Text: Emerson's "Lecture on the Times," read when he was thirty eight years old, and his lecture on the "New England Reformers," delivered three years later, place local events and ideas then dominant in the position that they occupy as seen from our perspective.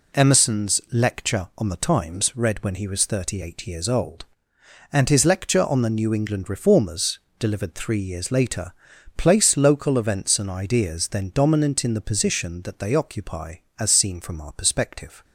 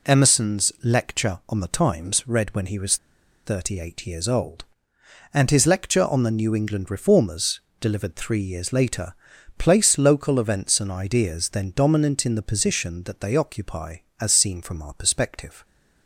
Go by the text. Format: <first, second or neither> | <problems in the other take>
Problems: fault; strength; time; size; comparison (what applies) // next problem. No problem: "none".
first | pauses between "was" and "thirty"; noticeable; at 2.9 s; 0.48 s long